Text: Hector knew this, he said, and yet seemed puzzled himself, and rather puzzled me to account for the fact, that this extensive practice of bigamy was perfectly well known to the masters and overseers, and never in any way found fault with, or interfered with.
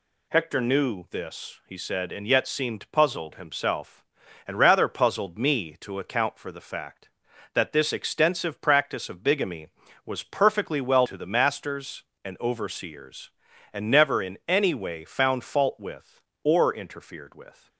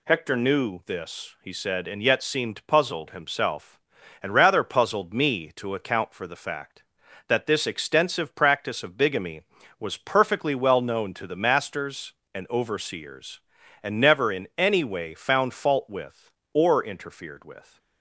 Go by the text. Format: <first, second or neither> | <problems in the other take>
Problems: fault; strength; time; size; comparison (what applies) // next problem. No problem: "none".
second | skips "known"; at 11.0 s